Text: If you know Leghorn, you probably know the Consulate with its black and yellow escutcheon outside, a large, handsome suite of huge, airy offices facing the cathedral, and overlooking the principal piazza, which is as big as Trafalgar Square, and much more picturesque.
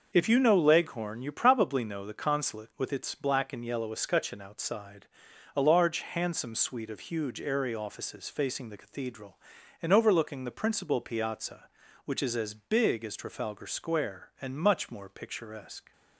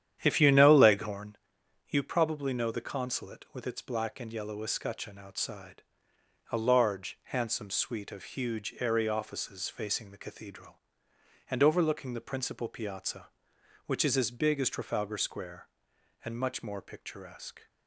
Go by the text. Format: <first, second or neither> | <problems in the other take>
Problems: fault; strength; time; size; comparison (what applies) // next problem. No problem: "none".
first | starts louder than the rest; strong; until 1.2 s; 10 dB